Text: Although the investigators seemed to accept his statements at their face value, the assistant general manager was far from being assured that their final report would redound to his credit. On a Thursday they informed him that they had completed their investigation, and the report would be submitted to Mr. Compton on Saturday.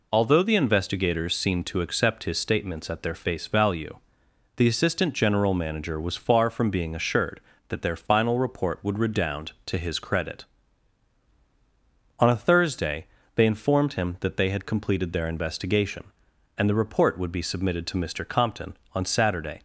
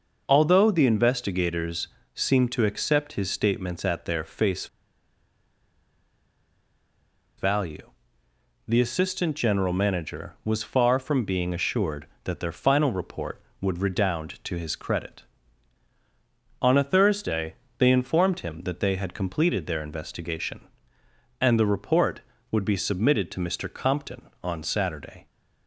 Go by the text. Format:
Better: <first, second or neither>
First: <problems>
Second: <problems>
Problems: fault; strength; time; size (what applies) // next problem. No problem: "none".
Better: first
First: pauses between "Thursday" and "they"; slight; at 13.0 s; 0.28 s long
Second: pauses between "investigators" and "seemed"; slight; at 1.8 s; 0.26 s long // pauses between "face" and "value"; strong; at 4.6 s; 2.7 s long // pauses between "Thursday" and "they"; slight; at 17.5 s; 0.24 s long